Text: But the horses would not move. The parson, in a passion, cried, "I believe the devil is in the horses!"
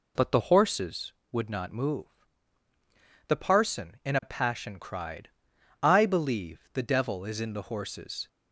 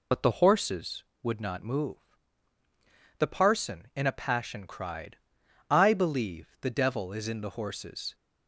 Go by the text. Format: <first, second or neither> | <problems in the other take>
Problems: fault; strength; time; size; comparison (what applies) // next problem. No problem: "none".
first | loses the start of "But"; at 0.1 s; 50 ms